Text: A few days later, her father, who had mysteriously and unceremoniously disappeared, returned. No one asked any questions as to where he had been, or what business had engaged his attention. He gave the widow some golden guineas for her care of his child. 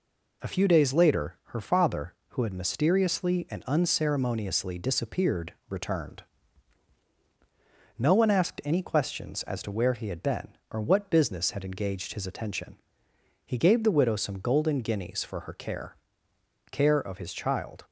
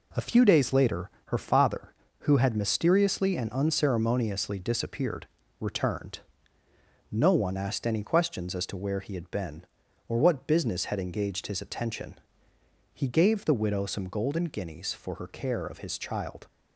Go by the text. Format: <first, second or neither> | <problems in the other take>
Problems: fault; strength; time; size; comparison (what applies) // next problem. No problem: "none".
second | says "care" twice; at 16.7 s